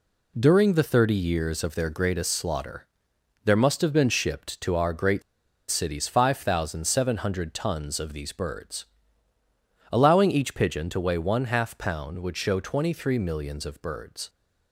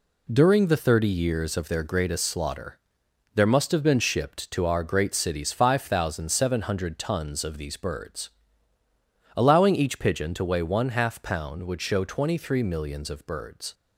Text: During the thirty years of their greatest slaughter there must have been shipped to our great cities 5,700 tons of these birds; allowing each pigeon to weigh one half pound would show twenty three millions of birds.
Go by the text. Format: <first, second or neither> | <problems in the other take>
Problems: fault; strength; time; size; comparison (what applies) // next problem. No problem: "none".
second | pauses between "slaughter" and "there"; noticeable; at 2.8 s; 0.58 s long; noticeable in the second // pauses between "great" and "cities"; noticeable; at 5.2 s; 0.48 s long